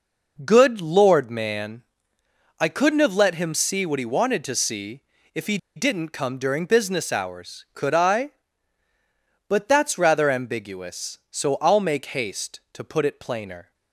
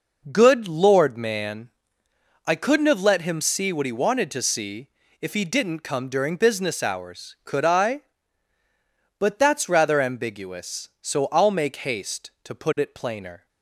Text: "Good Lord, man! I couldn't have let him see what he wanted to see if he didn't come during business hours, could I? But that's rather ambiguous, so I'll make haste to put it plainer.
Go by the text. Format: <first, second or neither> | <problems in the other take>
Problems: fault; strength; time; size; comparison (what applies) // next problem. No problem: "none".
second | pauses between "see" and "if"; slight; at 5.0 s; 0.32 s long; slight in the second // pauses between "he" and "didn't"; slight; at 5.5 s; 0.19 s long